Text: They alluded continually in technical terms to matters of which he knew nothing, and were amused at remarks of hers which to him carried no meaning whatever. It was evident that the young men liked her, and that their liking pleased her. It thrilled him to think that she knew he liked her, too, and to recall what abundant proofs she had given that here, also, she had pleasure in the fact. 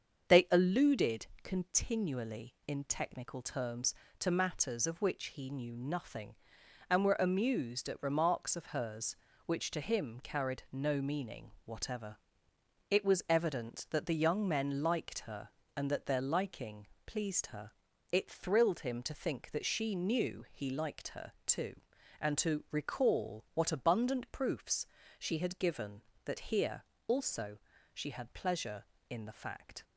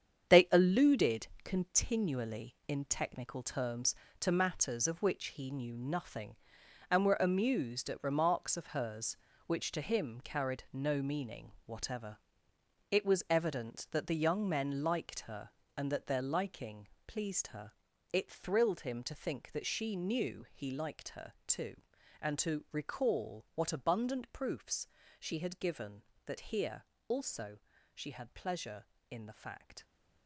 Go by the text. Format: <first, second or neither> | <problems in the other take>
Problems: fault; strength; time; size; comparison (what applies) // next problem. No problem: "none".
first | gets quieter; strong; throughout; 8.5 dB // starts louder than the rest; strong; until 1.5 s; 8 dB; also in the first // pauses between "alluded" and "continually"; slight; at 1.2 s; 0.18 s long; slight in the first // pauses between "meaning" and "whatever"; slight; at 11.5 s; 0.16 s long; slight in the first // pauses between "liking" and "pleased"; slight; at 16.8 s; 0.18 s long; slight in the first // pauses between "proofs" and "she"; slight; at 24.8 s; 0.34 s long; slight in the first